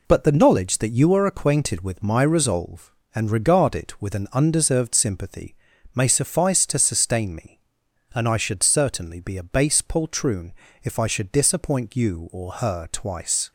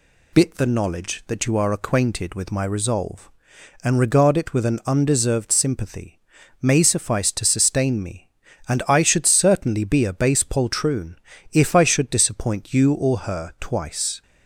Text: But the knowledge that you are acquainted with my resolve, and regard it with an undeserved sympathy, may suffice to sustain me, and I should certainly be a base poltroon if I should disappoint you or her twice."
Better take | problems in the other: first | says "Bit" for "But"; at 0.3 s // pauses between "poltroon" and "if"; at 11.1 s; 0.38 s long; slight in the first

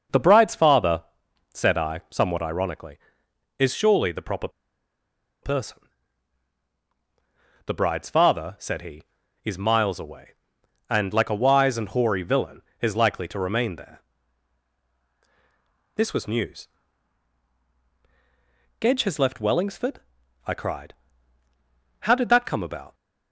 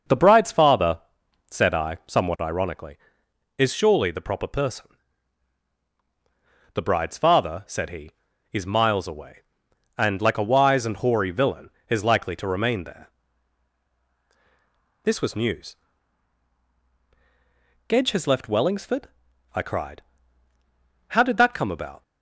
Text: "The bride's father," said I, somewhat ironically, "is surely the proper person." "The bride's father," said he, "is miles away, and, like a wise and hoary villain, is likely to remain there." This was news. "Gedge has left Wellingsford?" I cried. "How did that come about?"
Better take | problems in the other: second | pauses between "proper" and "person"; noticeable; at 4.4 s; 0.94 s long

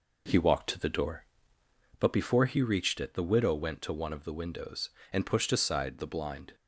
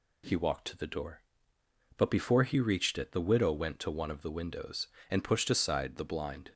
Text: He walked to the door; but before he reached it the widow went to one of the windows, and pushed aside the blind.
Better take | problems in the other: second | starts louder than the rest; noticeable; until 2.1 s; 5 dB

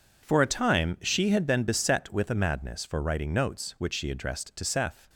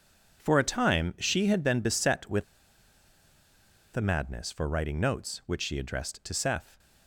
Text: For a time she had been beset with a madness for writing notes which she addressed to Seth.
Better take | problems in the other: first | pauses between "with" and "a"; strong; at 2.4 s; 1.5 s long

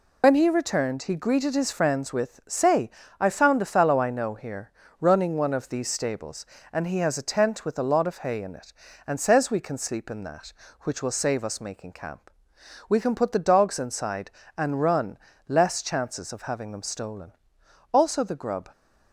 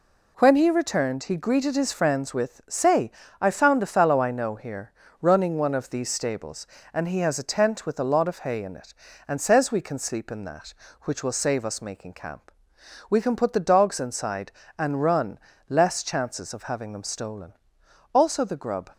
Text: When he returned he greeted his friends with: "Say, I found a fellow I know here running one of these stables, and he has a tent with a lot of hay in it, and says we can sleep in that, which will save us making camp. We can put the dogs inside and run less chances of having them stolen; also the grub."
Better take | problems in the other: second | loses the start of "When"; at 0.2 s; 85 ms // pauses between "here" and "running"; slight; at 4.7 s; 0.28 s long; slight in the second // pauses between "run" and "less"; slight; at 15.1 s; 0.28 s long; slight in the second

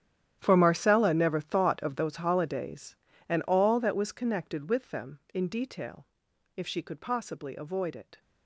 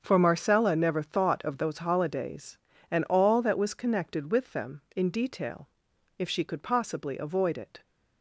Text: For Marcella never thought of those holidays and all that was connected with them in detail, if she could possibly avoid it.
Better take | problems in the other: second | gets quieter; strong; throughout; 17 dB // starts louder than the rest; strong; until 1.4 s; 10 dB; also in the second

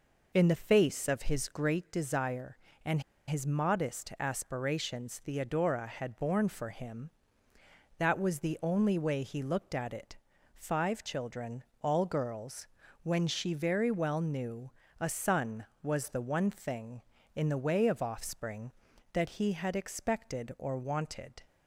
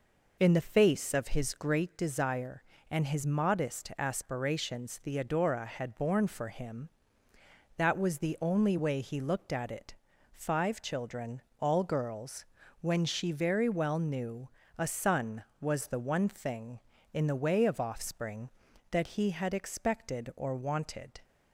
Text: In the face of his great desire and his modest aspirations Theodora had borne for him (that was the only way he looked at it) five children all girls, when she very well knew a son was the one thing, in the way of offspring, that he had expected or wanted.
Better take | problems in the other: second | pauses between "and" and "his"; slight; at 3.0 s; 0.25 s long // pauses between "children" and "all"; slight; at 11.6 s; 0.20 s long; slight in the second // pauses between "knew" and "a"; slight; at 14.7 s; 0.28 s long; slight in the second

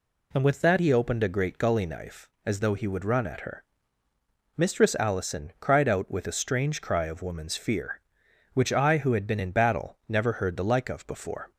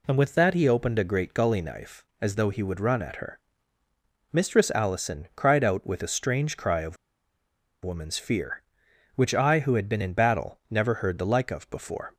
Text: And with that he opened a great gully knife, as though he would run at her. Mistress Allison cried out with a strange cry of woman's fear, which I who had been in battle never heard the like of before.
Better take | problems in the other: first | pauses between "of" and "woman's"; noticeable; at 6.9 s; 0.88 s long

